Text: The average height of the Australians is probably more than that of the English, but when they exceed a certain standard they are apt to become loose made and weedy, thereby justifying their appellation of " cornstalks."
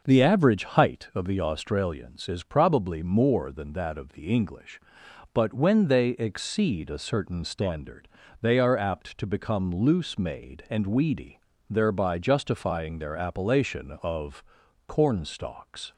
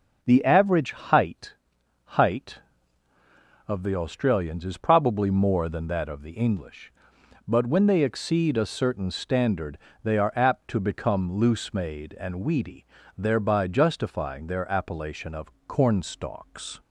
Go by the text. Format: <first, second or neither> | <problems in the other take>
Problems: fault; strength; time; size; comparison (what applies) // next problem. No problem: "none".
first | says "height" twice; at 2.0 s // pauses between "standard" and "they"; slight; at 9.7 s; 0.26 s long; slight in the first